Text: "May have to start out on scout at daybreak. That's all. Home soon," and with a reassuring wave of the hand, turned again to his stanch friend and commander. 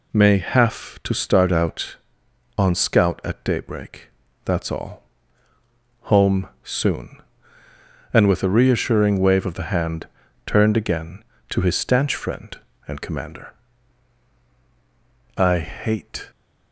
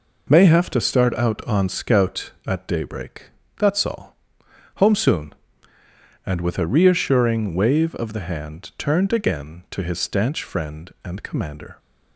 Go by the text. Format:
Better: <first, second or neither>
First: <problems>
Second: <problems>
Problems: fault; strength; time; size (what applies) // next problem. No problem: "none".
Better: second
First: pauses between "Home" and "soon"; slight; at 6.4 s; 0.16 s long // goes on to say "I hate"; noticeable; from 15.3 s on; 0.94 s long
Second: none